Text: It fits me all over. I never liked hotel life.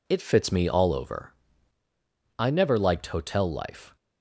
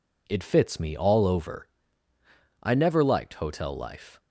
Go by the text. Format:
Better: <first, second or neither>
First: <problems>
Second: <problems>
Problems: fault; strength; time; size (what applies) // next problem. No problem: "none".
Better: neither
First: none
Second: none